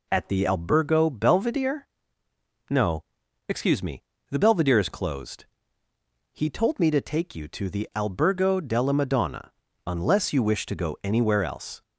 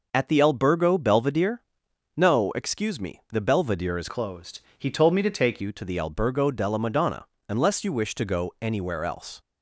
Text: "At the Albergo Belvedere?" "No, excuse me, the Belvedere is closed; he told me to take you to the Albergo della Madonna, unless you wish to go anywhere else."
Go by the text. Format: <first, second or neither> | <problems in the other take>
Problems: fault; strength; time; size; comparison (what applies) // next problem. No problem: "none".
first | changes voice from "closed" to "take"; from 4.0 to 5.6 s; 1.6 s long